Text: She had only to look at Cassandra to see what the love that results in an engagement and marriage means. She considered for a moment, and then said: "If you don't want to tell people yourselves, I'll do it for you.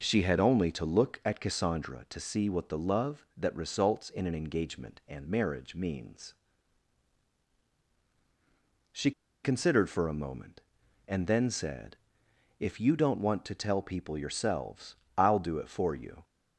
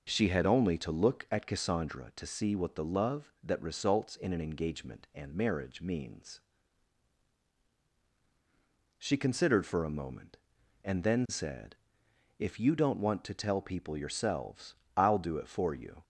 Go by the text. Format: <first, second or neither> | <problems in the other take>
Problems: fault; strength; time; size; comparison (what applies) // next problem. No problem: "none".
second | pauses between "She" and "considered"; slight; at 9.1 s; 0.32 s long